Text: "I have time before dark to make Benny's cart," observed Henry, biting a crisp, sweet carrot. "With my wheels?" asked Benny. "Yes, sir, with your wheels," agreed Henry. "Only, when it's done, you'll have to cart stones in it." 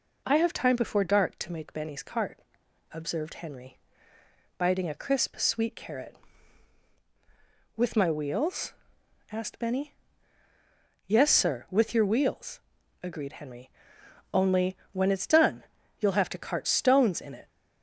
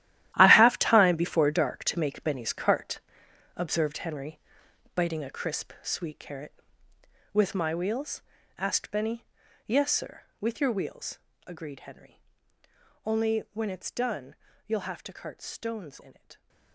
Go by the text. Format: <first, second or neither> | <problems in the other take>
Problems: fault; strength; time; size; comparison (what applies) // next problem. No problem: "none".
first | gets quieter; strong; throughout; 14 dB